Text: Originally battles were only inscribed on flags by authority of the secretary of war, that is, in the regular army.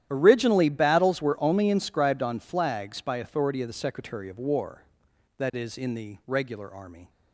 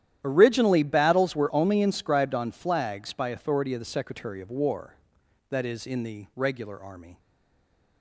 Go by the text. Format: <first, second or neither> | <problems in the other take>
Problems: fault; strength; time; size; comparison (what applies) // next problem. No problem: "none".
first | starts louder than the rest; strong; until 1.2 s; 11.5 dB; strong in the first // stays silent after the last word; slight; from 7.1 s on; 0.9 s long